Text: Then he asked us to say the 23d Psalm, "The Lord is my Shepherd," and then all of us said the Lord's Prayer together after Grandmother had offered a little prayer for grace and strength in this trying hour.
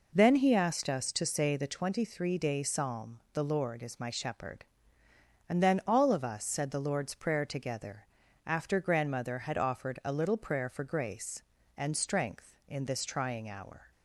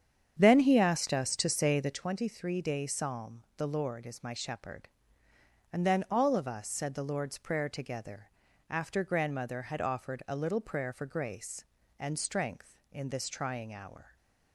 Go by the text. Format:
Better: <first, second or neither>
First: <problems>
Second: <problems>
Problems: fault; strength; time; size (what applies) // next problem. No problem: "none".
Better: first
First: pauses between "together" and "after"; at 8.0 s; 0.40 s long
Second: starts louder than the rest; strong; until 2.0 s; 8 dB // pauses between "together" and "after"; at 8.2 s; 0.40 s long